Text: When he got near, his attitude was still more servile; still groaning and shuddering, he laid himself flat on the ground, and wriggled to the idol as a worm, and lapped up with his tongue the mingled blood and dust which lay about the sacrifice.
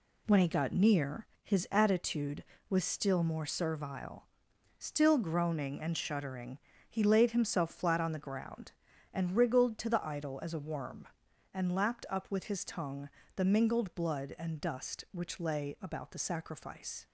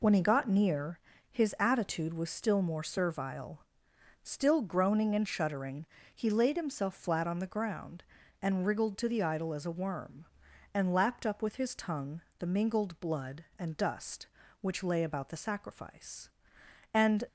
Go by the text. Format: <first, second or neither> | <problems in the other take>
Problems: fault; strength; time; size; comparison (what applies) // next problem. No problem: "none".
first | pauses between "tongue" and "the"; slight; at 12.2 s; 0.20 s long; slight in the first // goes on to say "And"; slight; from 16.9 s on; 0.32 s long